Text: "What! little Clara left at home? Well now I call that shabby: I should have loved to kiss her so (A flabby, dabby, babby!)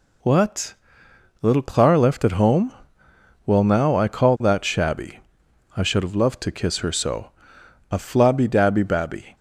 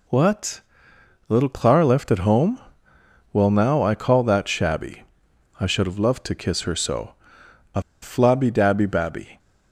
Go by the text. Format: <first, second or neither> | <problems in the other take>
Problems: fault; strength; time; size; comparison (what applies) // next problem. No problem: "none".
first | pauses between "A" and "flabby"; slight; at 7.8 s; 0.21 s long